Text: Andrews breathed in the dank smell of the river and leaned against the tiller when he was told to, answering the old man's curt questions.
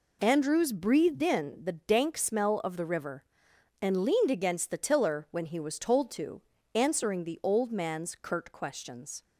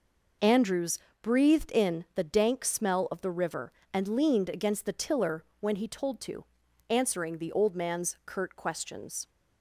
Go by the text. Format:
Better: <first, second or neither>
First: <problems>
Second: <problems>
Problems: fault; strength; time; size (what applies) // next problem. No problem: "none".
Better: first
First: none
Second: pauses between "Andrews" and "breathed"; slight; at 0.9 s; 0.22 s long // pauses between "tiller" and "when"; slight; at 5.4 s; 0.16 s long // skips "was"; at 5.8 s